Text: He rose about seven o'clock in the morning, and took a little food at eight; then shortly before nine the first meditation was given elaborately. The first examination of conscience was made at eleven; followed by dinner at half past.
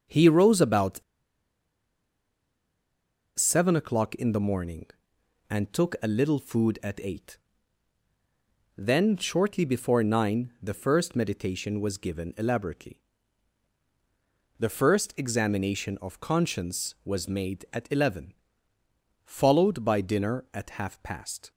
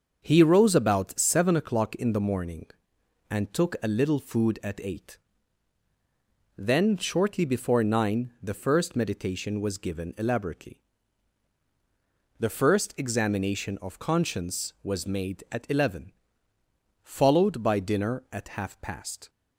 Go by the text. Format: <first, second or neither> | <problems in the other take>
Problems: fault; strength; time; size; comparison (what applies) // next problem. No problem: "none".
second | starts louder than the rest; until 3.4 s; 6.5 dB; also in the second // pauses between "about" and "seven"; strong; at 1.0 s; 2.3 s long